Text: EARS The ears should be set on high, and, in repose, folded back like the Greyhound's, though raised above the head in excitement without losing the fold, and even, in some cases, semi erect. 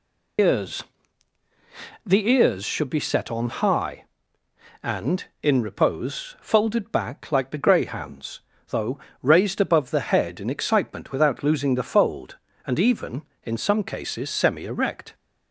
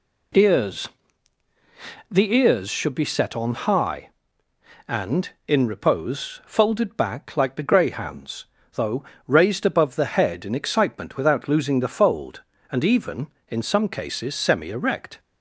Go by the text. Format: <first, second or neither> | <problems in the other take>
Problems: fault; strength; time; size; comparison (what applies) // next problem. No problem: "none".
second | loses the start of "EARS"; at 0.3 s; 115 ms // pauses between "EARS" and "The"; at 0.8 s; 1.2 s long; also in the second // pauses between "though" and "raised"; slight; at 8.9 s; 0.24 s long; slight in the second